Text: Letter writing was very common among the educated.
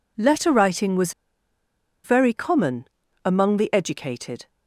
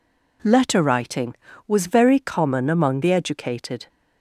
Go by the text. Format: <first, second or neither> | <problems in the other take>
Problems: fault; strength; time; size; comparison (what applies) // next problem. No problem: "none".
second | pauses between "was" and "very"; noticeable; at 1.1 s; 0.91 s long // pauses between "common" and "among"; slight; at 2.8 s; 0.36 s long